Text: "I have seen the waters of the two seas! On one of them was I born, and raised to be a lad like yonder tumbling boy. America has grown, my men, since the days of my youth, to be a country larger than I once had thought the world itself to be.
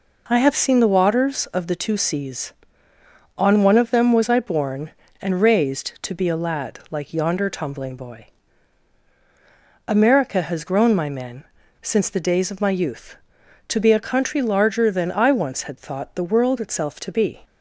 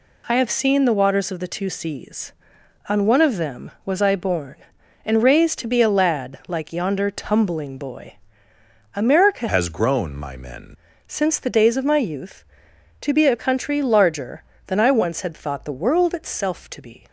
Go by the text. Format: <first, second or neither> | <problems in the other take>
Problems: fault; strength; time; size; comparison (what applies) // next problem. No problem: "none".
first | changes voice from "has" to "men"; from 9.4 to 10.7 s; 1.3 s long